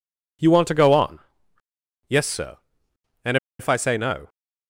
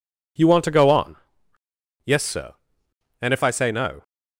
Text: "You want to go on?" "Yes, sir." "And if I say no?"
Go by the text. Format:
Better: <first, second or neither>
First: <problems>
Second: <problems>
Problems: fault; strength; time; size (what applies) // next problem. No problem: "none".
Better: second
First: pauses between "And" and "if"; slight; at 3.3 s; 0.23 s long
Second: none